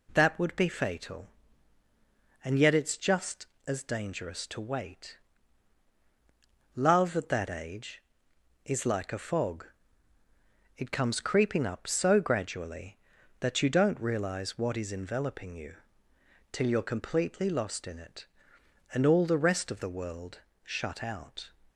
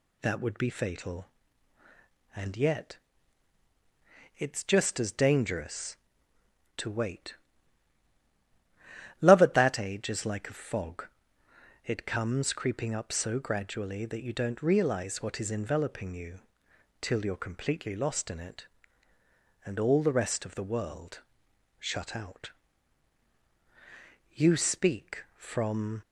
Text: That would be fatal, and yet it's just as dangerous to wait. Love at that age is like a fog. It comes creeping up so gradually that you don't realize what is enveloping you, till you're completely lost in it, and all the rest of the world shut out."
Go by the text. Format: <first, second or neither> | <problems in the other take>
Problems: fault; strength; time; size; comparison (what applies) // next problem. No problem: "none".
first | pauses between "yet" and "it's"; strong; at 2.9 s; 1.4 s long // pauses between "world" and "shut"; noticeable; at 21.2 s; 0.58 s long; slight in the first // goes on to say "You speak from"; strong; from 24.3 s on; 1.6 s long